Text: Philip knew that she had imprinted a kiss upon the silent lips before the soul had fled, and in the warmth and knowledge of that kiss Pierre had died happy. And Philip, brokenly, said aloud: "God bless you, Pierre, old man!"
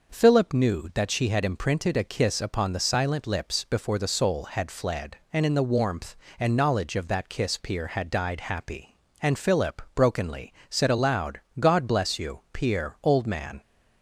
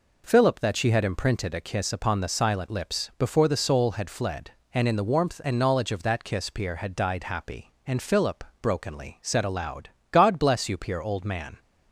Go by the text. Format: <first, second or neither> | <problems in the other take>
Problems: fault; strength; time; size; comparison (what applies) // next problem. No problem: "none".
first | skips "knew"; at 0.5 s